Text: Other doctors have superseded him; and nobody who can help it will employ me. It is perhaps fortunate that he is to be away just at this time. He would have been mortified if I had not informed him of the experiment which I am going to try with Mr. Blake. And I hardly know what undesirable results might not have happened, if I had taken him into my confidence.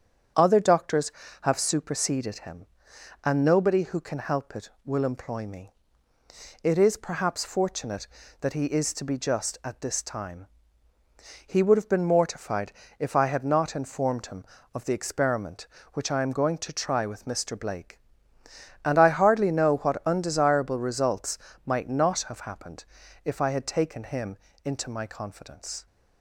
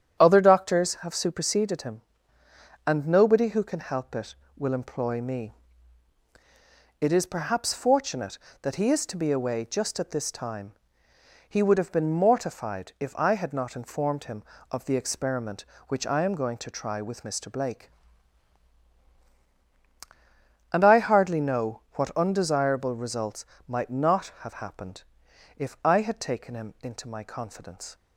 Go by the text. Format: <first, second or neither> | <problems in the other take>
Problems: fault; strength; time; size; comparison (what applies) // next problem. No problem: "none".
second | starts louder than the rest; strong; until 1.6 s; 8 dB; strong in the second // skips "away"; at 9.1 s // pauses between "mortified" and "if"; slight; at 12.7 s; 0.26 s long // pauses between "results" and "might"; slight; at 21.3 s; 0.26 s long; slight in the second // pauses between "him" and "into"; slight; at 24.3 s; 0.28 s long